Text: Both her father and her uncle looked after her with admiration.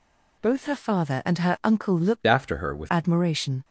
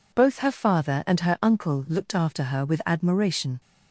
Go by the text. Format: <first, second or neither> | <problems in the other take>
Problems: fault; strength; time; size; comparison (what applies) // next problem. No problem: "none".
second | changes voice from "after" to "with"; from 2.2 to 2.8 s; 0.6 s long